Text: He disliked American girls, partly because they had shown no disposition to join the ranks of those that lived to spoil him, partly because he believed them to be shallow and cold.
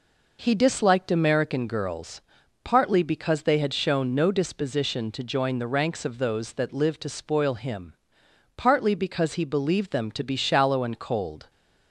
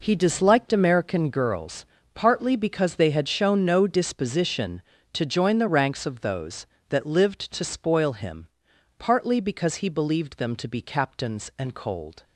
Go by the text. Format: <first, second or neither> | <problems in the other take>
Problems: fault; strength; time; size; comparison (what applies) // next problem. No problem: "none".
first | says "captains" for "shallow"; at 10.8 s